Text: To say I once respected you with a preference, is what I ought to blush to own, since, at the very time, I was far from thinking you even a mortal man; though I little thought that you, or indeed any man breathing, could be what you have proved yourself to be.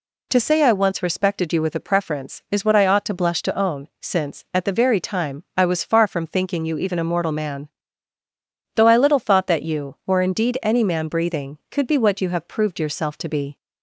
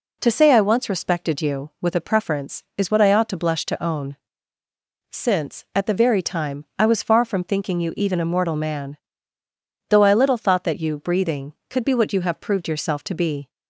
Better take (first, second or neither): first